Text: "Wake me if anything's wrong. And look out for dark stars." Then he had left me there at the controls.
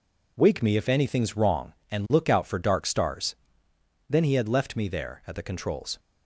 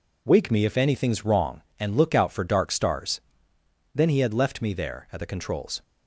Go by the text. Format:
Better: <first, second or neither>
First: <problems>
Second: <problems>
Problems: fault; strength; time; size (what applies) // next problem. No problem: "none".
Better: neither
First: none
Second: none